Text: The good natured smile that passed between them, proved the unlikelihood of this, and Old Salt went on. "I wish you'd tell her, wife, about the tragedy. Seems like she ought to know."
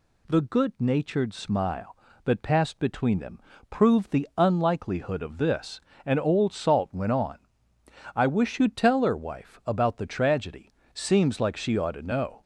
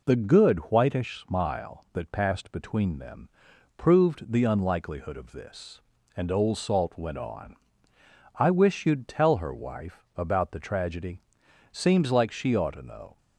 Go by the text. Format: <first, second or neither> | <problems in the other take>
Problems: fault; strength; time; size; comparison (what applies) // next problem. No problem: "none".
first | says "whitish" for "natured"; at 0.7 s